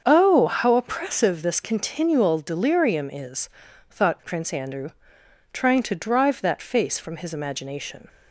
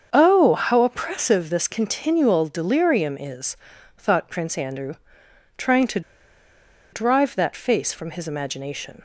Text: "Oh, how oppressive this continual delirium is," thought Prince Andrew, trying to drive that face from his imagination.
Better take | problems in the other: first | starts louder than the rest; until 1.1 s; 7 dB; also in the first // pauses between "to" and "drive"; noticeable; at 6.0 s; 0.92 s long

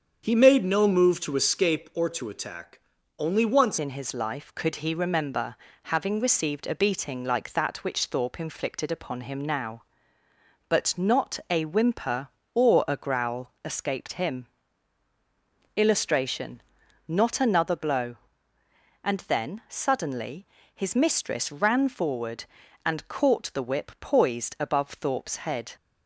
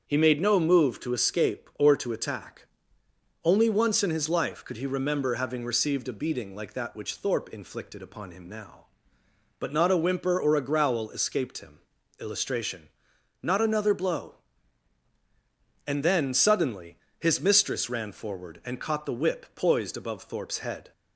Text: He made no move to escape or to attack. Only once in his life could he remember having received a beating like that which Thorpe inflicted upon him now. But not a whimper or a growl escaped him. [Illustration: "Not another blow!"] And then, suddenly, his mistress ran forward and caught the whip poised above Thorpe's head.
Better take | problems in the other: second | starts louder than the rest; strong; until 1.2 s; 7.5 dB; also in the second // changes voice at "in"; from 3.7 s on; 22.0 s long // pauses between "remember" and "having"; slight; at 5.5 s; 0.36 s long

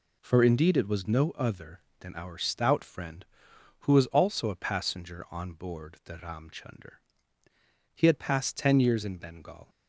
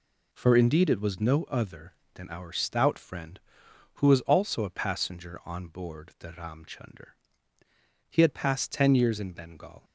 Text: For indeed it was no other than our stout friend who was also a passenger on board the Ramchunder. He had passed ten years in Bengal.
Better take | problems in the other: neither | none

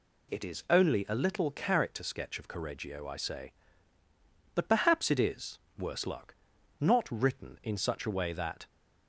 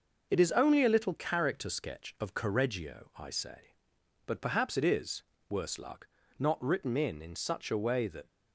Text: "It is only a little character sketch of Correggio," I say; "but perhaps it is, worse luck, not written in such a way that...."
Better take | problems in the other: first | says "in" twice; at 7.2 s

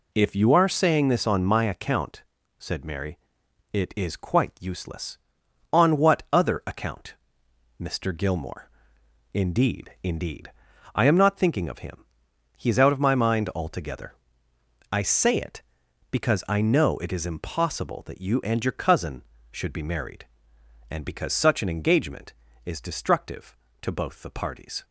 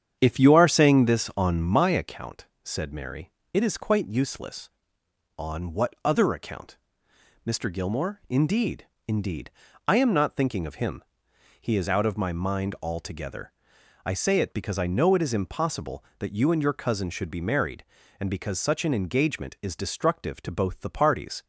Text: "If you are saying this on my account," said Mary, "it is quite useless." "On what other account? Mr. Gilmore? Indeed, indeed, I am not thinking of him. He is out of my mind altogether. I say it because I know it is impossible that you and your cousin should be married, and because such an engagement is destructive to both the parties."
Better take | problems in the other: first | starts louder than the rest; strong; until 2.1 s; 8 dB

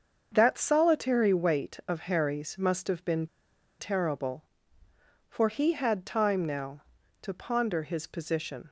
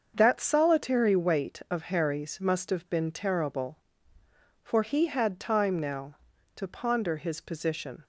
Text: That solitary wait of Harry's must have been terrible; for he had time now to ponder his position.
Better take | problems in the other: second | starts louder than the rest; until 1.3 s; 6.5 dB; also in the second // pauses between "been" and "terrible"; noticeable; at 3.2 s; 0.52 s long

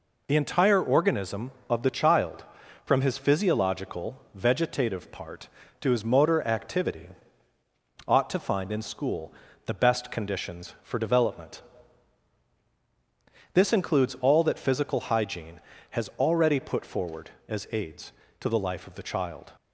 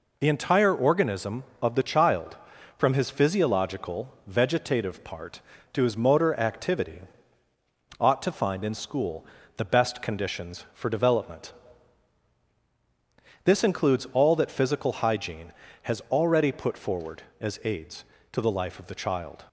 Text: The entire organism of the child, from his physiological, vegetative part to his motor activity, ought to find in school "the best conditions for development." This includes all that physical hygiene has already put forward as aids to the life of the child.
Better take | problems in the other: neither | pauses between "school" and "the"; slight; the same in both

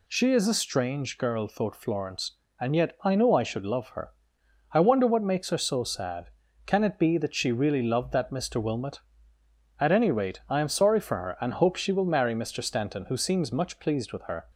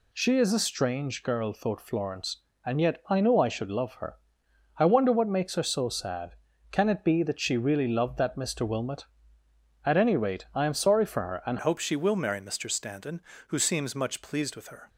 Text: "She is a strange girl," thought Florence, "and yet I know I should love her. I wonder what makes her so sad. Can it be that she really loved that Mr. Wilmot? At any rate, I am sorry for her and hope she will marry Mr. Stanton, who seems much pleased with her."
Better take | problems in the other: first | changes voice at "hope"; from 11.6 s on; 3.2 s long

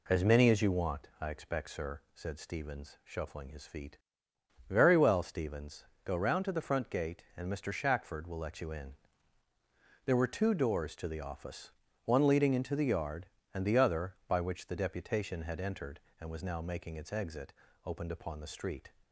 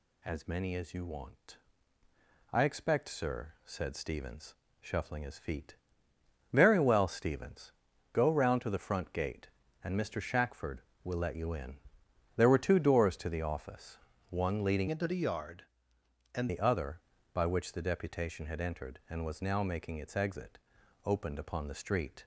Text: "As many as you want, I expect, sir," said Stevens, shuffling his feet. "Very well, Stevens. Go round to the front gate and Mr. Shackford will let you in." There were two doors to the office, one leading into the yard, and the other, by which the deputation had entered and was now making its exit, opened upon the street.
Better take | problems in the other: first | changes voice from "into" to "and"; from 14.8 to 16.4 s; 1.6 s long

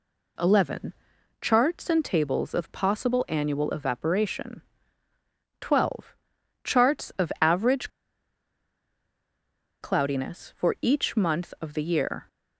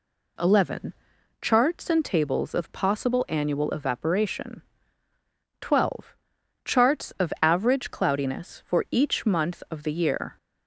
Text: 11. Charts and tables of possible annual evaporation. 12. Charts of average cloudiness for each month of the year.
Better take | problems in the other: second | pauses between "average" and "cloudiness"; strong; at 7.8 s; 1.9 s long

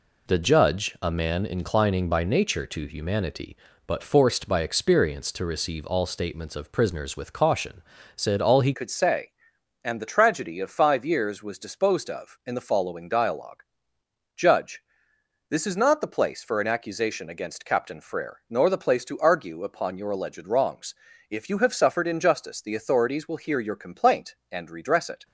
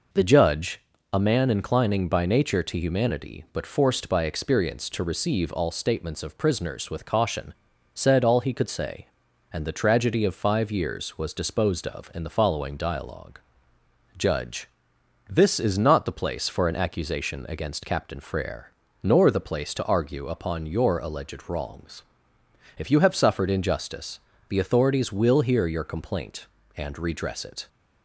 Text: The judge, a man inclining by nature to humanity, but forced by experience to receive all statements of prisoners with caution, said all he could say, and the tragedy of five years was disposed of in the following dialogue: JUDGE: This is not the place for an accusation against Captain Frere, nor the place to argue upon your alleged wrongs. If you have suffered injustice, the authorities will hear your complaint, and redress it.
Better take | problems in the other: second | changes voice at "could"; from 8.7 s on; 16.5 s long

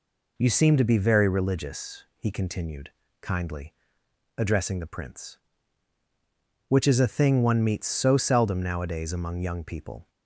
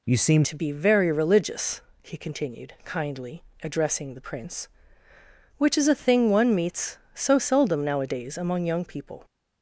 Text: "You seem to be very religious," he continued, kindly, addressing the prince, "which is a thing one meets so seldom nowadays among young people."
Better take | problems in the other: first | changes voice at "to"; from 0.4 s on; 8.8 s long

